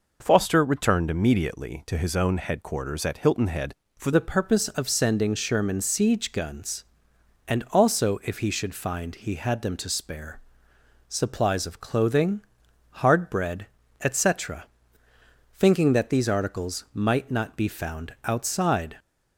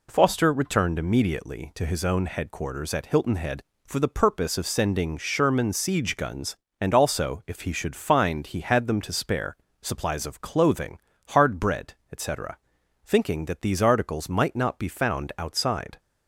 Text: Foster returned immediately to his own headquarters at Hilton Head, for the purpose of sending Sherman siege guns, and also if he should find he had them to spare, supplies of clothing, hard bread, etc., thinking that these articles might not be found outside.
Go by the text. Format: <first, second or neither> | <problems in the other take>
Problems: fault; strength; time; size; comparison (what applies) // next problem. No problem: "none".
second | changes voice at "the"; from 4.1 s on; 14.8 s long